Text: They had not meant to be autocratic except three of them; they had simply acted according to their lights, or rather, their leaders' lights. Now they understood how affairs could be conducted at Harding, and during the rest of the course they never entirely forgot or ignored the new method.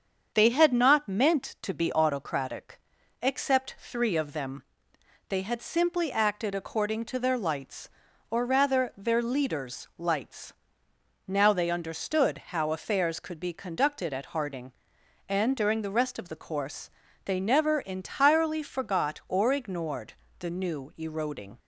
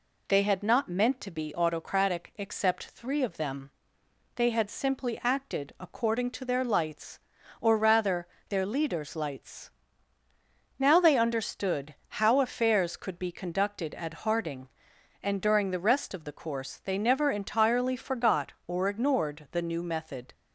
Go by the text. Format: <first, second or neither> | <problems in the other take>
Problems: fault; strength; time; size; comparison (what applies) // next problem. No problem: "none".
second | starts louder than the rest; until 1.3 s; 7 dB // pauses between "autocratic" and "except"; at 2.8 s; 0.40 s long // pauses between "course" and "they"; slight; at 16.9 s; 0.34 s long // pauses between "ignored" and "the"; slight; at 20.1 s; 0.26 s long // says "eroding" for "method"; at 20.9 s